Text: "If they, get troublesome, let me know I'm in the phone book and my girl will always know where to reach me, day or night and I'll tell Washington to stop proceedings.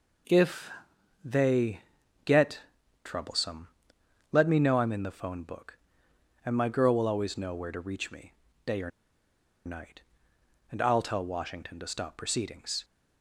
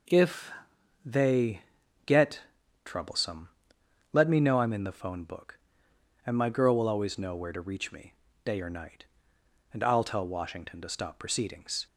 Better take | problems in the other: second | pauses between "If" and "they"; noticeable; at 0.7 s; 0.52 s long; noticeable in the second // pauses between "get" and "troublesome"; at 2.6 s; 0.42 s long; also in the second // pauses between "or" and "night"; noticeable; at 8.8 s; 0.76 s long

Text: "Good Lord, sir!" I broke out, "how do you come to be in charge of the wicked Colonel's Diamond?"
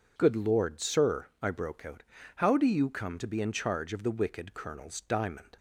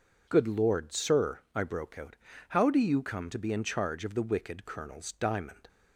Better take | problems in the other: neither | none

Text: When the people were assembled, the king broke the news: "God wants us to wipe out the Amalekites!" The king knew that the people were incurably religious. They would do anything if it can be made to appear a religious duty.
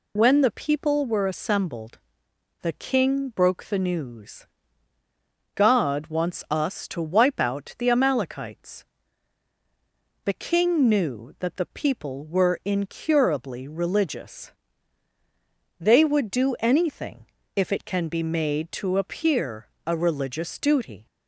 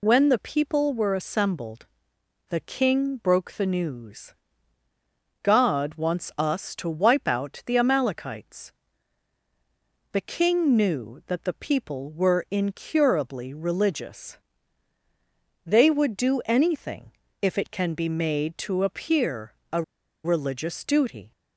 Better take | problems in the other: first | pauses between "anything" and "if"; slight; at 17.1 s; 0.28 s long; slight in the first // pauses between "appear" and "a"; slight; at 19.5 s; 0.18 s long; slight in the first // pauses between "a" and "religious"; at 19.8 s; 0.42 s long

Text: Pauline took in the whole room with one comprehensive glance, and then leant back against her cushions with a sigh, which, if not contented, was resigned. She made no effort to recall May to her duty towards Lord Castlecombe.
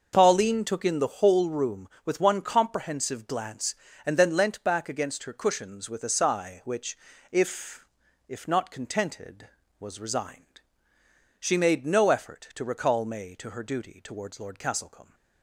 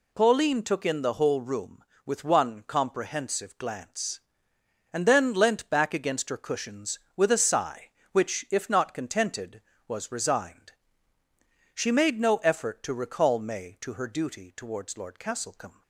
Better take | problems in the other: second | starts louder than the rest; until 1.1 s; 6 dB // says "if" twice; at 8.2 s

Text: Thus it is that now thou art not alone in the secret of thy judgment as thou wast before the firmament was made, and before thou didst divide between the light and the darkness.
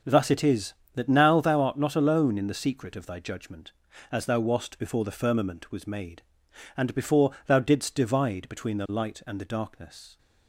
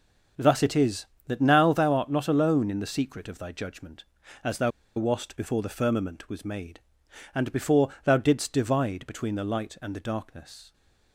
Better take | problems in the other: first | starts louder than the rest; until 1.6 s; 6.5 dB; also in the first // pauses between "thou" and "wast"; slight; at 4.7 s; 0.26 s long // pauses between "before" and "thou"; slight; at 7.8 s; 0.16 s long; slight in the first

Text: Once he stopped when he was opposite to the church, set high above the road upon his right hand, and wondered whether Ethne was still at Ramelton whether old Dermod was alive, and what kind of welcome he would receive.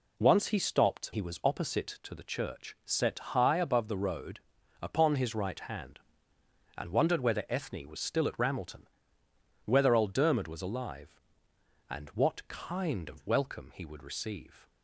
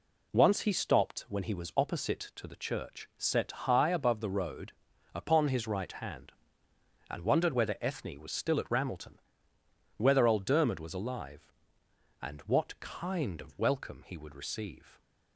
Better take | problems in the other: second | skips "when"; at 1.1 s // pauses between "road" and "upon"; at 4.3 s; 0.40 s long; also in the second // pauses between "Ramelton" and "whether"; noticeable; at 8.8 s; 0.80 s long; noticeable in the second

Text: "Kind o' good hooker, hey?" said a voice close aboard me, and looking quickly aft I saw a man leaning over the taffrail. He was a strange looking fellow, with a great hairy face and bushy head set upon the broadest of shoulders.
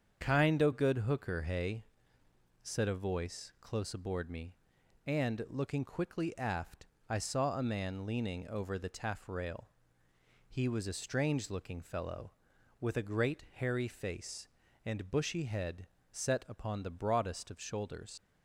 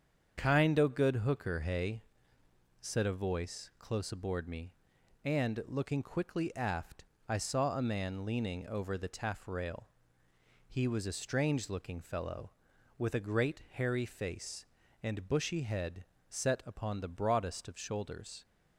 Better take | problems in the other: second | starts louder than the rest; strong; until 1.3 s; 7.5 dB; strong in the second // pauses between "aft" and "I"; slight; at 6.8 s; 0.22 s long; slight in the second // pauses between "head" and "set"; slight; at 15.8 s; 0.24 s long; slight in the second // leaves "shoulders" unfinished; at 18.1 s; 95 ms

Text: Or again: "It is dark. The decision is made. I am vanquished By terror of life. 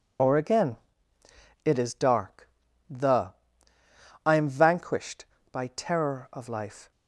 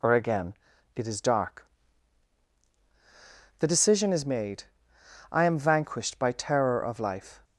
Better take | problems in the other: second | skips "decision is made"; at 3.7 s

